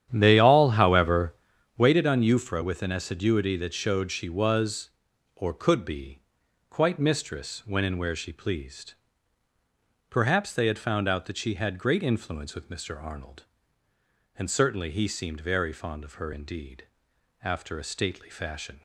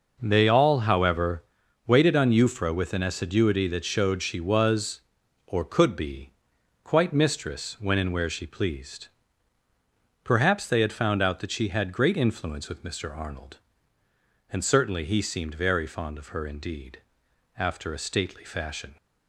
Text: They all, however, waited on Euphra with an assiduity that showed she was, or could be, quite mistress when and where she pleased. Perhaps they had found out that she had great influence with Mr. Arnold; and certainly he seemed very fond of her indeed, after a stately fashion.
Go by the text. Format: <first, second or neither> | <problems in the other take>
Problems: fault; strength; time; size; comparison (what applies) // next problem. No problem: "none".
second | starts louder than the rest; strong; until 2.0 s; 10 dB